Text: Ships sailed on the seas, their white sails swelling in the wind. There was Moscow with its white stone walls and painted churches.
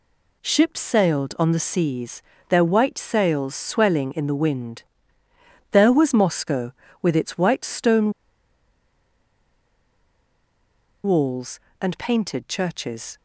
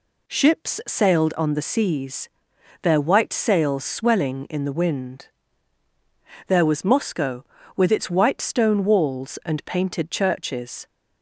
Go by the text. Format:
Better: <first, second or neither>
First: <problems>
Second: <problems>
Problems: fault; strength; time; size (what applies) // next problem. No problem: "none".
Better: second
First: pauses between "stone" and "walls"; strong; at 8.1 s; 2.9 s long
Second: none